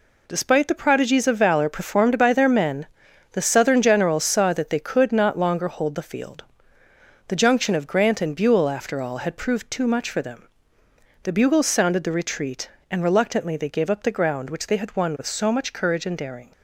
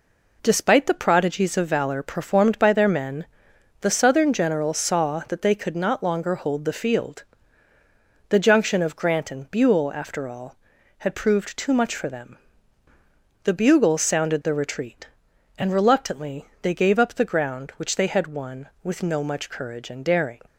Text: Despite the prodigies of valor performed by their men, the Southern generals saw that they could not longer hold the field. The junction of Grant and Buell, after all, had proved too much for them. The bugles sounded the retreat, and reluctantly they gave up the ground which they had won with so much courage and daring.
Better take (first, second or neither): first